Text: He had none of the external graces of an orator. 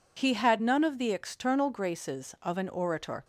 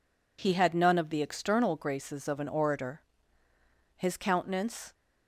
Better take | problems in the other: first | goes on to say "His countenance"; noticeable; from 3.9 s on; 0.96 s long

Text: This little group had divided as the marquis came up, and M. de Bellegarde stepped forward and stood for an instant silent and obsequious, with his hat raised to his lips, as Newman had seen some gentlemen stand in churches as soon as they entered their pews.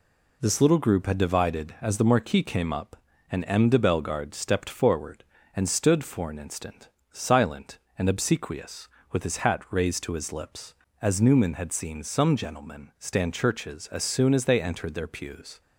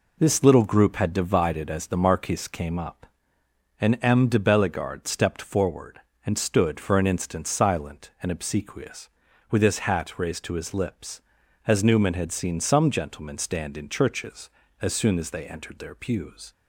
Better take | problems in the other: second | pauses between "instant" and "silent"; slight; at 6.8 s; 0.22 s long // skips "in"; at 13.3 s

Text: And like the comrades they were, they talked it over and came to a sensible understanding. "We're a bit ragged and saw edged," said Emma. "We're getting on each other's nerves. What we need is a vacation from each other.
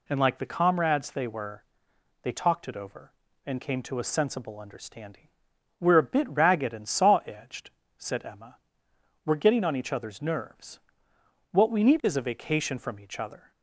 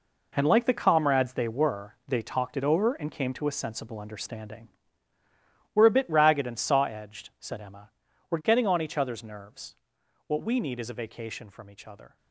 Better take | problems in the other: first | gets quieter; strong; throughout; 11.5 dB

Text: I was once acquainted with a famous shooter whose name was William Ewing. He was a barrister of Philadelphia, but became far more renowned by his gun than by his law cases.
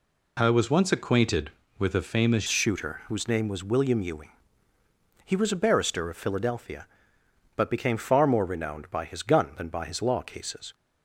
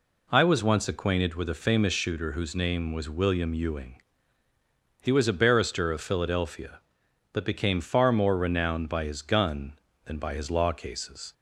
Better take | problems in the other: second | changes voice at "shooter"; from 2.4 s on; 8.3 s long

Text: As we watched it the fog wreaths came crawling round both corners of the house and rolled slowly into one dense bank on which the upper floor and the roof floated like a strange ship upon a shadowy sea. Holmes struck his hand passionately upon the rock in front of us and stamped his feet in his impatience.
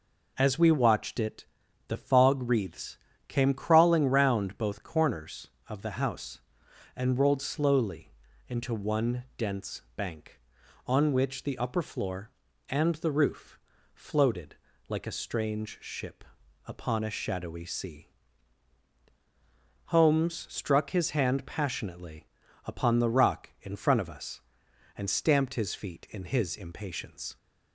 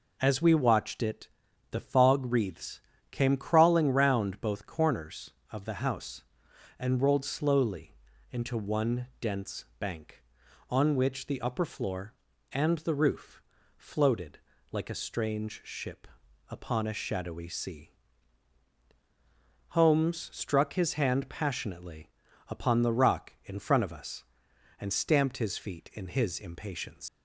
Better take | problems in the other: first | pauses between "it" and "the"; at 1.2 s; 0.42 s long; also in the first // pauses between "wreaths" and "came"; slight; at 2.7 s; 0.32 s long; slight in the first // pauses between "slowly" and "into"; at 7.9 s; 0.38 s long; also in the first // pauses between "roof" and "floated"; slight; at 13.4 s; 0.34 s long; slight in the first // pauses between "floated" and "like"; slight; at 14.3 s; 0.32 s long; slight in the first // pauses between "ship" and "upon"; at 16.0 s; 0.42 s long; also in the first // pauses between "passionately" and "upon"; at 22.0 s; 0.38 s long; also in the first // leaves "impatience" unfinished; at 27.0 s; 115 ms

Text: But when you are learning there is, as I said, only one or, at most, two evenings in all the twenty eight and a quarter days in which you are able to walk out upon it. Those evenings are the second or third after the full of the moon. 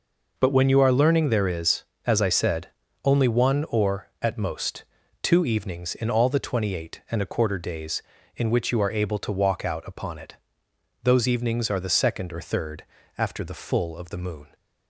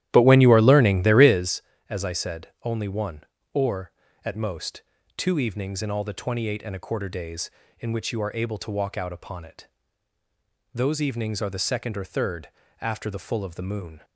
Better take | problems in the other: first | starts louder than the rest; strong; until 1.6 s; 13 dB // pauses between "third" and "after"; slight; at 12.4 s; 0.32 s long; slight in the first

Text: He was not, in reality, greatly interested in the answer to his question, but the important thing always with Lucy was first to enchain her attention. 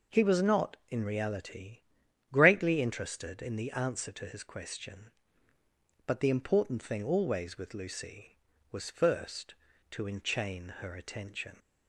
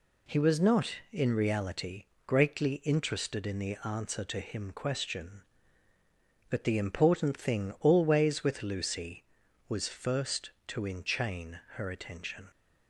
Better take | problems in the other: first | says "him" for "his"; at 4.4 s // pauses between "enchain" and "her"; slight; at 11.5 s; 0.16 s long

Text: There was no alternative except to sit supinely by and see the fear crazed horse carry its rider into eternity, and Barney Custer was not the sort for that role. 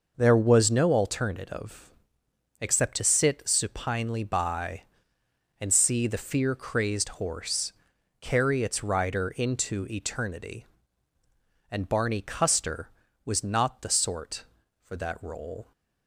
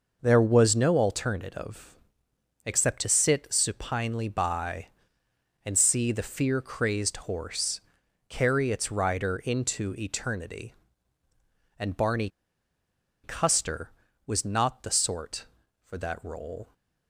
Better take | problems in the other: first | pauses between "alternative" and "except"; noticeable; at 1.9 s; 0.70 s long; noticeable in the first // pauses between "horse" and "carry"; noticeable; at 7.7 s; 0.48 s long; noticeable in the first // pauses between "Barney" and "Custer"; noticeable; at 12.2 s; 0.96 s long

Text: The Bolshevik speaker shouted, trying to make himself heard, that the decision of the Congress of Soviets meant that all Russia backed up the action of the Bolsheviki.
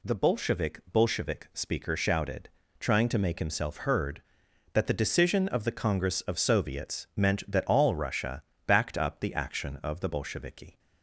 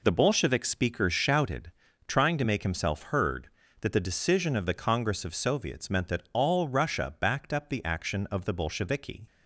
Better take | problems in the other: second | says "Bolshevik" twice; at 0.9 s // pauses between "Russia" and "backed"; slight; at 8.4 s; 0.22 s long

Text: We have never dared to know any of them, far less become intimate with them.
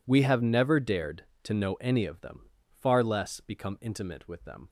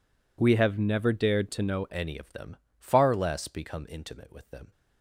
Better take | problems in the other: first | changes voice at "any"; from 1.8 s on; 2.9 s long

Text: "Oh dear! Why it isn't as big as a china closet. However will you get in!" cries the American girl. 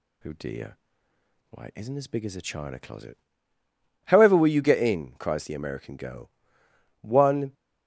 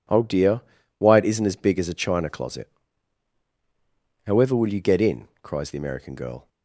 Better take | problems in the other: second | goes on to say "One"; from 7.0 s on; 0.52 s long

